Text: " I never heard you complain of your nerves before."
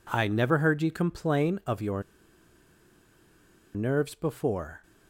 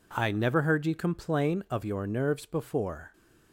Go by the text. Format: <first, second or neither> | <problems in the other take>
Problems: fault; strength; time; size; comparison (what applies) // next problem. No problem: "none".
second | pauses between "your" and "nerves"; strong; at 2.0 s; 1.7 s long